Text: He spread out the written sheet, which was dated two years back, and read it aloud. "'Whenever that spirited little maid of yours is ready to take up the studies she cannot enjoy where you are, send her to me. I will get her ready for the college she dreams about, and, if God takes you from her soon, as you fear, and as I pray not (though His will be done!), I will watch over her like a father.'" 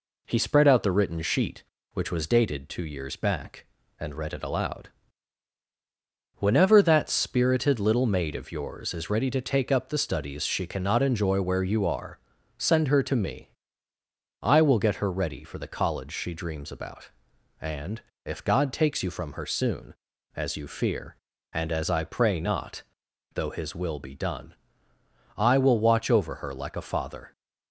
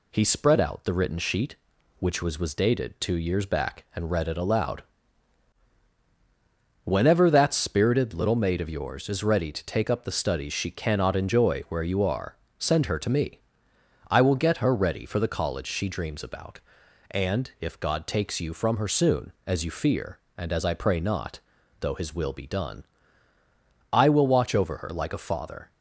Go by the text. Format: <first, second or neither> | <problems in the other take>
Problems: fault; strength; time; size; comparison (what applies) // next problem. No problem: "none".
first | says "was" twice; at 2.3 s